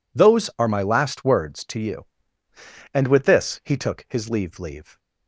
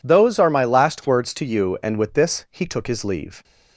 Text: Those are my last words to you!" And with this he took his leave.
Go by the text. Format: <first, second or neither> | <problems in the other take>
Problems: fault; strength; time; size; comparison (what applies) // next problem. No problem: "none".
second | says "leave" twice; at 4.5 s